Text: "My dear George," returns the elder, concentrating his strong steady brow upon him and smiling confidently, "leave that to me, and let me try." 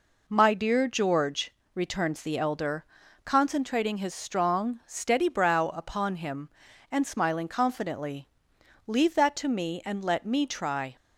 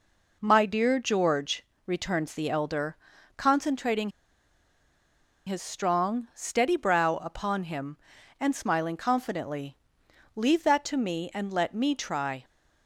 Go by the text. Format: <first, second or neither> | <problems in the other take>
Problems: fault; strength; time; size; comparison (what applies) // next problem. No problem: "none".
first | pauses between "concentrating" and "his"; strong; at 4.1 s; 1.3 s long